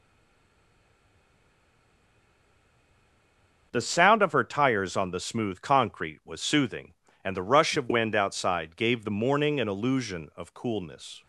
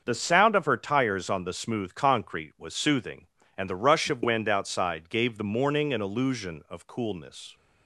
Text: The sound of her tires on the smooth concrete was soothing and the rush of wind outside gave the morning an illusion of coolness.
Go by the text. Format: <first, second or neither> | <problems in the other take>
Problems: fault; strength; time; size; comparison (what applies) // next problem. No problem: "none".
second | stays silent before the first word; strong; until 3.7 s; 3.7 s long // starts louder than the rest; until 4.7 s; 6.5 dB; also in the second